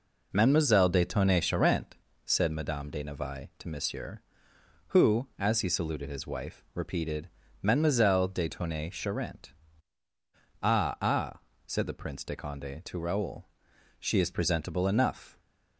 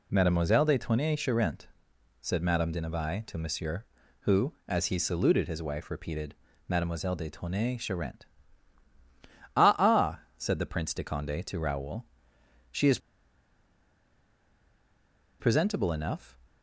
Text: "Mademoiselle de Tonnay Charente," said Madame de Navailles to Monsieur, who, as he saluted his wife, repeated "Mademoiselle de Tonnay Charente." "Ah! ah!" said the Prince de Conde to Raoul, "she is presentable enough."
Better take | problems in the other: first | pauses between "repeated" and "Mademoiselle"; slight; at 6.3 s; 0.32 s long; slight in the first // pauses between "is" and "presentable"; strong; at 12.9 s; 2.4 s long

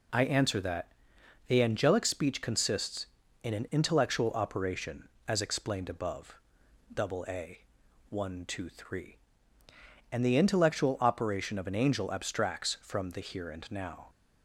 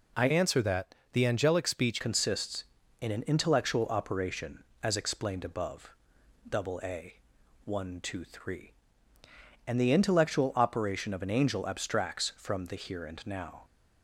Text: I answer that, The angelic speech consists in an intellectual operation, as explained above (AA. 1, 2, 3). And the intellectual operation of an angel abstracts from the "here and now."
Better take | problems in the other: first | changes voice from "answer" to "speech"; from 0.2 to 2.0 s; 1.8 s long

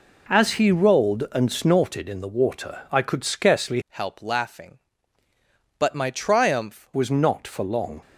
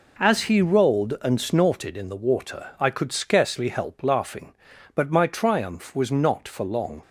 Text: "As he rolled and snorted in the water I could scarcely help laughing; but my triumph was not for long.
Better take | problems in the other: second | changes voice from "help" to "triumph"; from 3.8 to 6.8 s; 3.0 s long

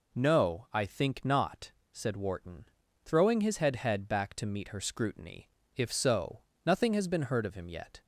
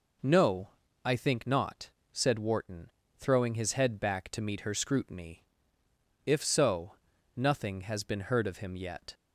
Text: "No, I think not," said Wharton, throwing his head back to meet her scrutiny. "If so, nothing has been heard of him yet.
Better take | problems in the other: second | says "head" twice; at 3.7 s

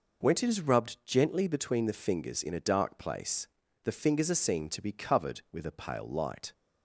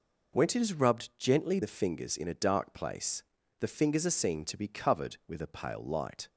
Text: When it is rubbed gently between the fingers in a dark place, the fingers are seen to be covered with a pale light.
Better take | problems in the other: first | skips "between"; at 1.6 s

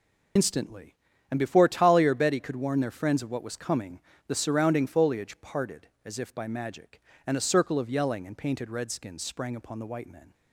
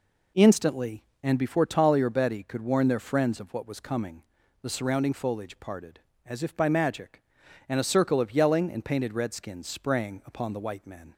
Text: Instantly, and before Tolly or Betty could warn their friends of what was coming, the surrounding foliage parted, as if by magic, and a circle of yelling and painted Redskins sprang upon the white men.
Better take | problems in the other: second | loses the start of "Instantly"; at 0.3 s; 65 ms

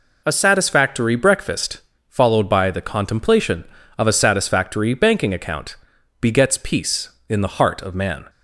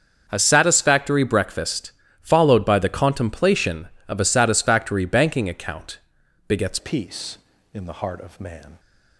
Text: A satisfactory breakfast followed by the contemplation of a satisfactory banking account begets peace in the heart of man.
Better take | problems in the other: first | starts louder than the rest; until 1.2 s; 6.5 dB // pauses between "breakfast" and "followed"; slight; at 1.9 s; 0.28 s long; slight in the first // pauses between "account" and "begets"; noticeable; at 5.9 s; 0.50 s long; also in the first // changes voice at "peace"; from 6.7 s on; 2.0 s long

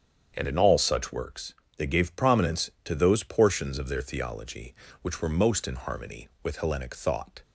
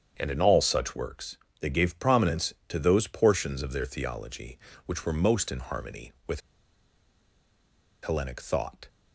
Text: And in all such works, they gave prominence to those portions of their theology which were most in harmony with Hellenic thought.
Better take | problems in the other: first | starts louder than the rest; strong; until 1.1 s; 8 dB; strong in the first // pauses between "with" and "Hellenic"; strong; at 6.4 s; 1.6 s long

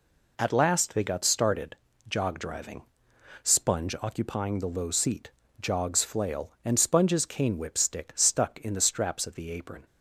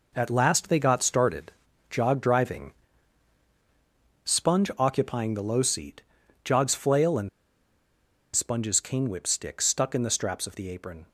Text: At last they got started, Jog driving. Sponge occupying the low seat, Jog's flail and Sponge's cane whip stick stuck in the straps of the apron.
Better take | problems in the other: first | pauses between "and" and "Sponge's"; at 7.2 s; 1.0 s long

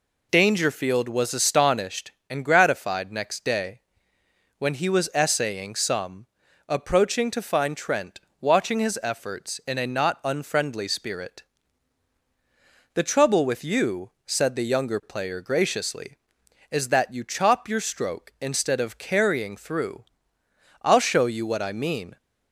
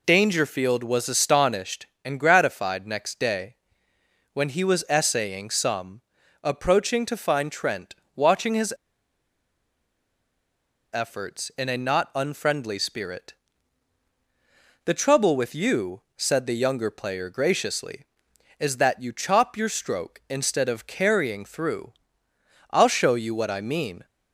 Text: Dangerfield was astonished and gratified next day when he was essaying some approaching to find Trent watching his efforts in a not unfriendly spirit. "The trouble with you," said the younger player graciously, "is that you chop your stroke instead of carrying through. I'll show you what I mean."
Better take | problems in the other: first | pauses between "day" and "when"; noticeable; at 3.5 s; 0.78 s long; noticeable in the first // pauses between "some" and "approaching"; at 6.0 s; 0.42 s long; also in the first // pauses between "Trent" and "watching"; slight; at 7.9 s; 0.20 s long; slight in the first // pauses between "his" and "efforts"; strong; at 8.7 s; 2.1 s long

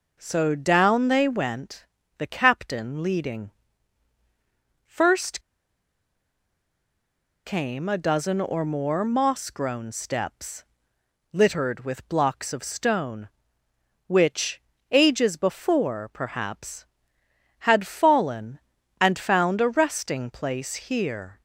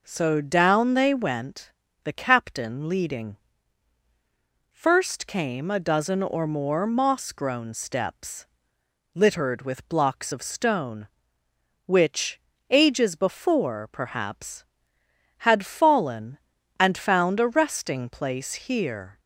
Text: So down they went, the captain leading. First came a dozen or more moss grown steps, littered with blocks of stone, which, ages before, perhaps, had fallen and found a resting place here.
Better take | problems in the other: second | pauses between "First" and "came"; strong; at 5.3 s; 2.0 s long

